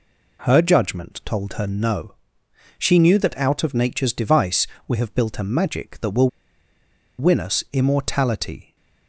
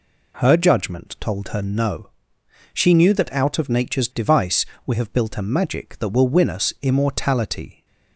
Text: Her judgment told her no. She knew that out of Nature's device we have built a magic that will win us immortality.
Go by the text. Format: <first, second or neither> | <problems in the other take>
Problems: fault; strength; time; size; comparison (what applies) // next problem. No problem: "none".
second | pauses between "device" and "we"; slight; at 4.6 s; 0.22 s long; slight in the second // pauses between "will" and "win"; noticeable; at 6.2 s; 0.89 s long